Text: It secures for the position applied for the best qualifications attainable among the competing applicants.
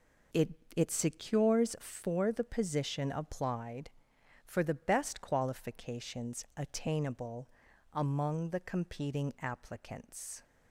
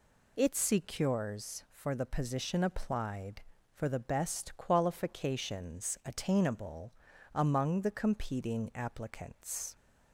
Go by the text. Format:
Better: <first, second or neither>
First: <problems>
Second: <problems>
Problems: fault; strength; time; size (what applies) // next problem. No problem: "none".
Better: second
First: says "It" twice; at 0.7 s // pauses between "attainable" and "among"; at 7.4 s; 0.44 s long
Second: pauses between "attainable" and "among"; at 6.9 s; 0.40 s long